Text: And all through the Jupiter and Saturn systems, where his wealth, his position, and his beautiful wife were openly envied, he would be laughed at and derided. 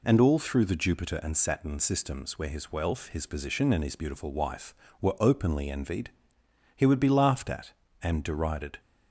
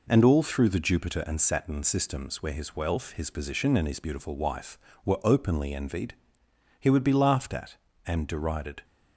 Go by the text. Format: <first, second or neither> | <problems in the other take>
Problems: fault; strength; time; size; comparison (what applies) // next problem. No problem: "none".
first | gets quieter; noticeable; throughout; 4 dB